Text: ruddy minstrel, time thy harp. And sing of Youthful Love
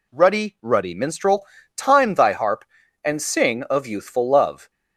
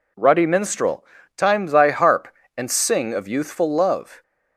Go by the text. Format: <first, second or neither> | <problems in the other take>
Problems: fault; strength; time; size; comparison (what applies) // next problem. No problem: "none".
second | says "ruddy" twice; at 0.6 s